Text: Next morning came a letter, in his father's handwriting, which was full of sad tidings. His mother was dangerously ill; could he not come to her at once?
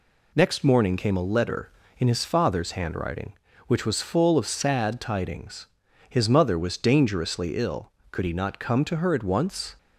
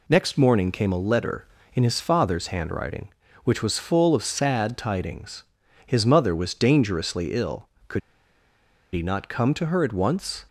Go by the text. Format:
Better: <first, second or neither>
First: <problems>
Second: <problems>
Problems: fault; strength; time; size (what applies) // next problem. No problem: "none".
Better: first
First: none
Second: pauses between "could" and "he"; noticeable; at 8.0 s; 0.95 s long